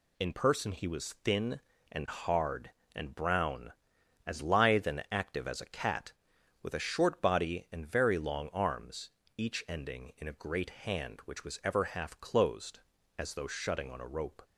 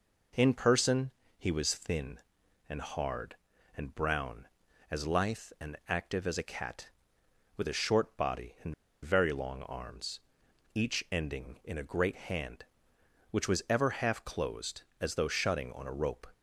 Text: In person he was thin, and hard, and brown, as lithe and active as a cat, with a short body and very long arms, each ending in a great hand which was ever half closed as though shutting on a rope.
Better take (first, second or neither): first